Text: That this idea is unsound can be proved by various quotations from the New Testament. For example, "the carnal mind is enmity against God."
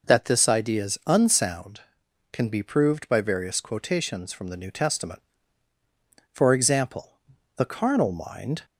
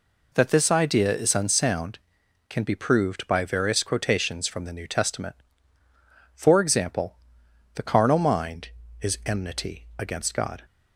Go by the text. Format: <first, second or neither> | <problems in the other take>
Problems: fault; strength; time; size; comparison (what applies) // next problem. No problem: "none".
second | stops before "is enmity against God"; at 8.6 s